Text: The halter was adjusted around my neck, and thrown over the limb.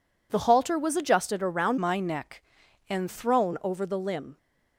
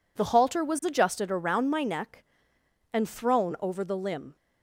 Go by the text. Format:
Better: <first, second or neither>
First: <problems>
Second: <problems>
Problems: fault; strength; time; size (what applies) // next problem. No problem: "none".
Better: second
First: changes voice from "my" to "and"; from 1.7 to 3.0 s; 1.3 s long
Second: none